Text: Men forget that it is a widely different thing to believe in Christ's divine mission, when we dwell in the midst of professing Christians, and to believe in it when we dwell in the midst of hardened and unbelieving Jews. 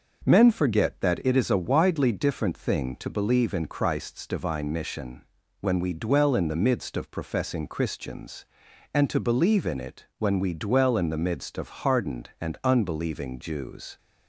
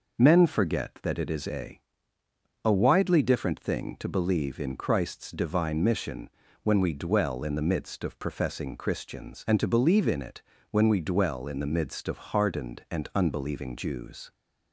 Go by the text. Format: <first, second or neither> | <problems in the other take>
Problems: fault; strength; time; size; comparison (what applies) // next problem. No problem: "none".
first | says "a" twice; at 2.6 s // pauses between "it" and "when"; slight; at 10.4 s; 0.26 s long